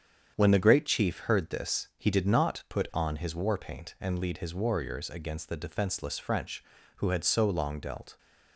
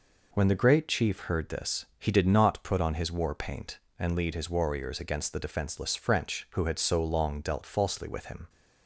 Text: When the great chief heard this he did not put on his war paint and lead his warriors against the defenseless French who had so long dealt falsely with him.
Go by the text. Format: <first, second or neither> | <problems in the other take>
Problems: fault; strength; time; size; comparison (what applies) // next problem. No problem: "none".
second | starts louder than the rest; strong; until 1.3 s; 8 dB // stops before "falsely with him"; at 8.1 s